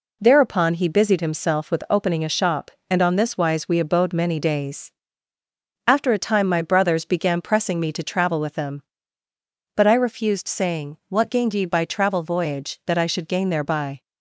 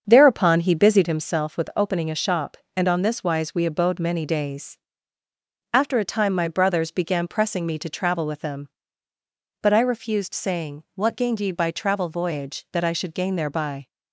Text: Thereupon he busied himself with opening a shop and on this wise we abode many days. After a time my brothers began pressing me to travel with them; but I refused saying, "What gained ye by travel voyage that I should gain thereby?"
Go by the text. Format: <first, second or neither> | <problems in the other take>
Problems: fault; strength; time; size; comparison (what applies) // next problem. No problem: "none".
first | starts louder than the rest; until 1.3 s; 7 dB